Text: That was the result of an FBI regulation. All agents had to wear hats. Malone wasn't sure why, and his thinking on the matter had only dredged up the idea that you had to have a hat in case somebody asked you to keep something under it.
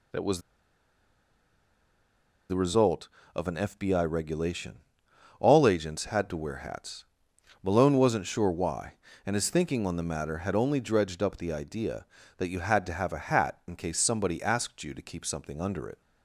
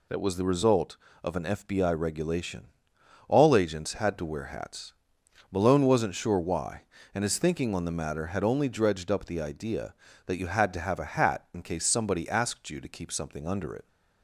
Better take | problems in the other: second | pauses between "was" and "the"; strong; at 0.4 s; 2.0 s long

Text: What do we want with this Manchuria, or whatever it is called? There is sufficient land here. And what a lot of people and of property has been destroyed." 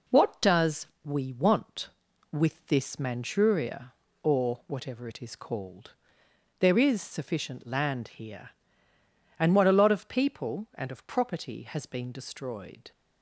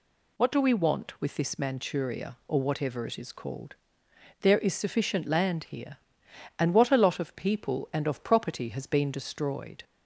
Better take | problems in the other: second | says "does" for "do"; at 0.4 s

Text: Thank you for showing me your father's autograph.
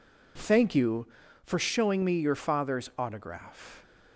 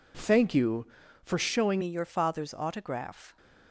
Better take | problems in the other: first | changes voice at "me"; from 1.8 s on; 1.5 s long

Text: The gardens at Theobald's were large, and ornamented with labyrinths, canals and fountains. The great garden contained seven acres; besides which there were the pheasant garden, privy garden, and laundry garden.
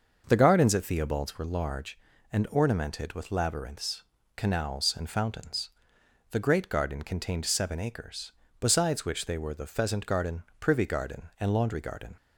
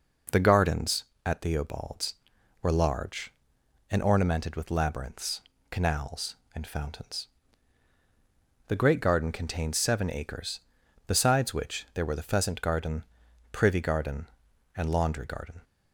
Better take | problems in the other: second | starts louder than the rest; until 1.2 s; 6 dB // says "they" for "there"; at 9.2 s

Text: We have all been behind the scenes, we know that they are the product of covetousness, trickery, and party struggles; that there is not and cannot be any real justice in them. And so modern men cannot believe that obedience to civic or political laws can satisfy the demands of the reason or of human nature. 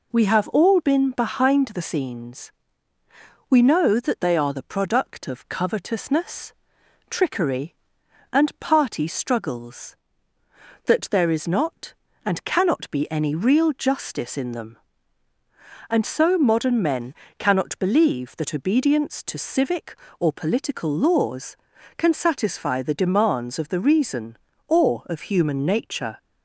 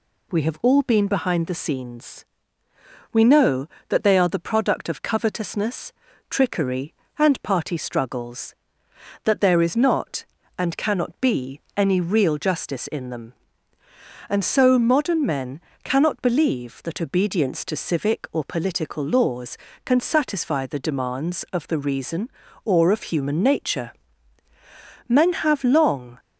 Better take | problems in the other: first | pauses between "be" and "any"; slight; at 11.5 s; 0.16 s long // pauses between "men" and "cannot"; slight; at 15.5 s; 0.24 s long; slight in the first // goes on to say "Men have long"; noticeable; from 25.0 s on; 1.1 s long

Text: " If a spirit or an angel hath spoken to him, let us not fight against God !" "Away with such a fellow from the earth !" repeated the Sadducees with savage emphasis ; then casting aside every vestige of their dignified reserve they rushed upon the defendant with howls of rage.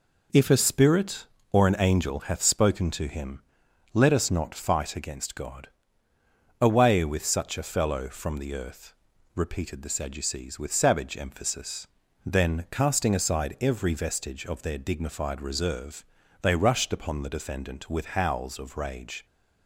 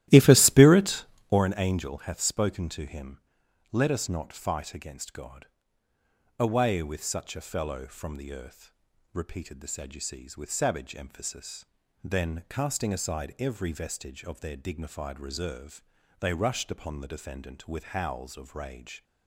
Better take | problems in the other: first | starts louder than the rest; strong; until 1.4 s; 14.5 dB // pauses between "reserve" and "they"; at 15.8 s; 0.38 s long; also in the first

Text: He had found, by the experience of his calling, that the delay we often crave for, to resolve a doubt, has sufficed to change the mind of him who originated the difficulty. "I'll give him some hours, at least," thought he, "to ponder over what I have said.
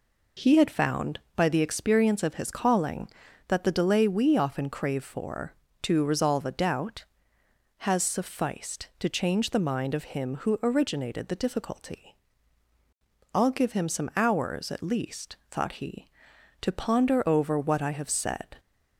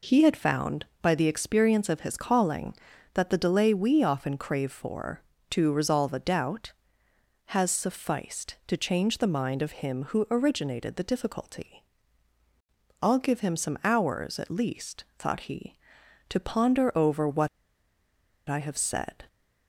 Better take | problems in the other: first | pauses between "what" and "I"; at 17.4 s; 0.99 s long

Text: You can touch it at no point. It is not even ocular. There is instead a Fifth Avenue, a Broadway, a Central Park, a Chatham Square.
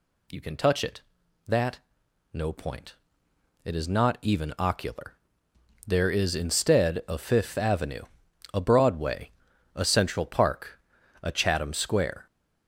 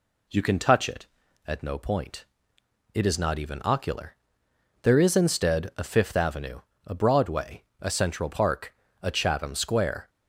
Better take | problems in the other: second | says "that" for "at"; at 1.4 s

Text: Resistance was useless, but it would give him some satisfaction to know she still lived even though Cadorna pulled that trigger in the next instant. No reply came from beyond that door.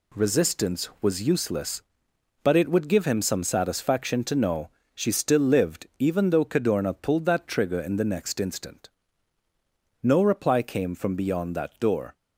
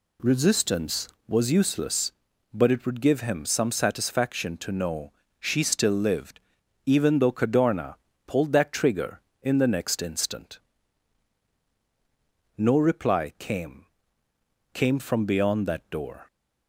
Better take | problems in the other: first | pauses between "know" and "she"; slight; at 5.1 s; 0.26 s long; slight in the first // pauses between "lived" and "even"; noticeable; at 6.3 s; 0.46 s long // pauses between "Cadorna" and "pulled"; slight; at 7.9 s; 0.32 s long // says "came" twice; at 14.7 s

